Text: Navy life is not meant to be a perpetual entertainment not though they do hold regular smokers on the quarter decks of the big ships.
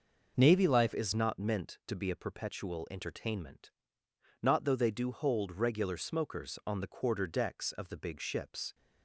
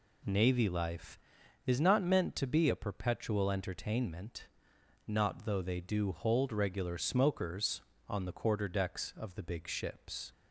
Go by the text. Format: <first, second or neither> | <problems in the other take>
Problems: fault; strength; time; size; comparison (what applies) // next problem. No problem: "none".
second | changes voice at "is"; from 0.9 s on; 7.8 s long // pauses between "entertainment" and "not"; noticeable; at 3.7 s; 0.72 s long; noticeable in the second